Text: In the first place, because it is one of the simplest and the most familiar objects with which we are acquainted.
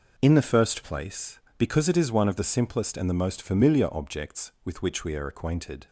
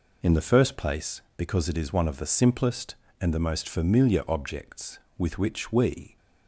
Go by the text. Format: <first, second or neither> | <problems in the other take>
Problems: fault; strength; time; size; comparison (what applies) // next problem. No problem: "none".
first | stops before "are acquainted"; at 6.1 s